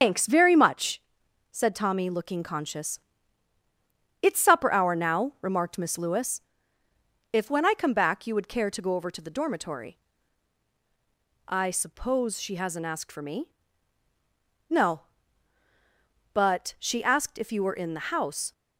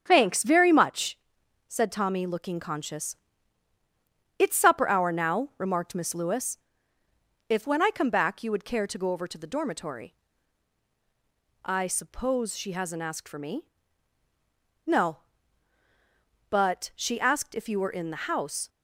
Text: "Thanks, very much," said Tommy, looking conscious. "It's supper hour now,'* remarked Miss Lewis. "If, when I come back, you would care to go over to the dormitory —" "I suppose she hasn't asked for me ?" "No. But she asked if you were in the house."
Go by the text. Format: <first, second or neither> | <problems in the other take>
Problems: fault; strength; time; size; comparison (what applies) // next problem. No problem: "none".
second | loses the start of "Thanks"; at 0.0 s; 120 ms // starts louder than the rest; until 1.0 s; 6.5 dB; strong in the second